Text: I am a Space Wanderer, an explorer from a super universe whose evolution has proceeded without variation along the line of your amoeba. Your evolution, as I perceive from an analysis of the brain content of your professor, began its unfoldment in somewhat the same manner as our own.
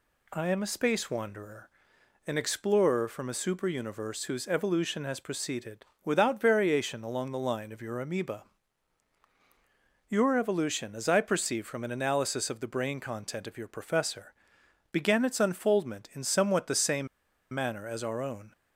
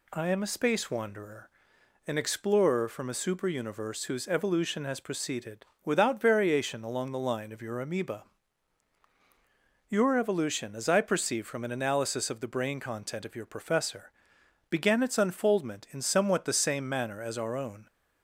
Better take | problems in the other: second | pauses between "proceeded" and "without"; slight; at 5.8 s; 0.18 s long; slight in the second // pauses between "same" and "manner"; noticeable; at 17.0 s; 0.46 s long

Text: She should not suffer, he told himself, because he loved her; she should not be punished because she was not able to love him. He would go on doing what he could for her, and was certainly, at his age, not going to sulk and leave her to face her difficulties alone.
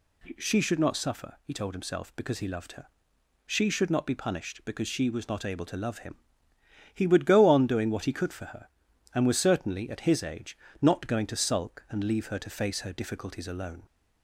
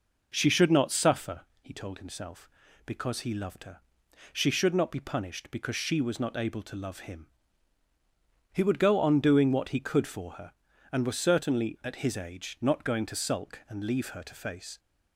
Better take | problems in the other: first | stops before "her difficulties alone"; at 14.7 s

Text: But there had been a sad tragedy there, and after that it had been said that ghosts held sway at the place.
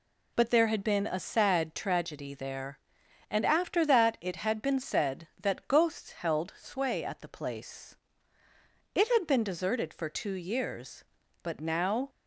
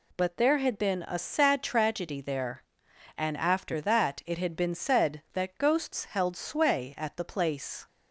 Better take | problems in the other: second | goes on to say "It had been deserted for two years but now"; strong; from 8.9 s on; 3.1 s long

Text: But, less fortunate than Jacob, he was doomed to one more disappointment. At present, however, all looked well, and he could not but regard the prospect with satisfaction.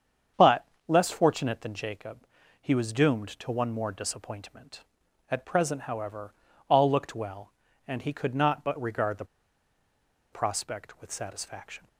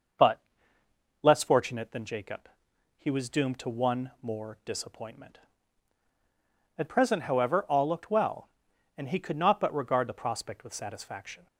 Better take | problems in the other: second | starts louder than the rest; strong; until 1.5 s; 7.5 dB // pauses between "the" and "prospect"; at 9.2 s; 1.0 s long

